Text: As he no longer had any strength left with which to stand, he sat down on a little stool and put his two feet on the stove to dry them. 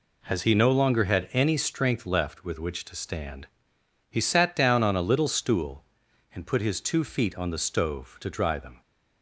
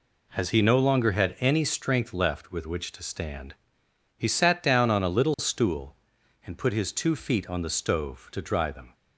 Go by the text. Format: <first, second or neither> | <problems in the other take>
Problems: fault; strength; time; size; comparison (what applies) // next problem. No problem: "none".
neither | none